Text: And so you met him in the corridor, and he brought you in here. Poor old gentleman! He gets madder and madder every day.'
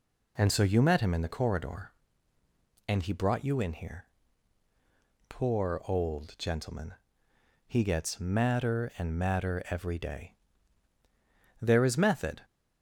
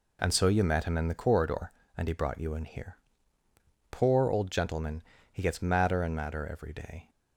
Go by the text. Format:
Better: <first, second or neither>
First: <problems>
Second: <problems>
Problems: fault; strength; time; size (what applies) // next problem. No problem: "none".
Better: second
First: goes on to say "There is method"; noticeable; from 11.6 s on; 0.80 s long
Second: none